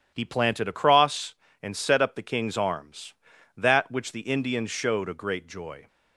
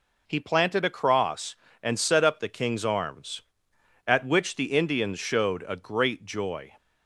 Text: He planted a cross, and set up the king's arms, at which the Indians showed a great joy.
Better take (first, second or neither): second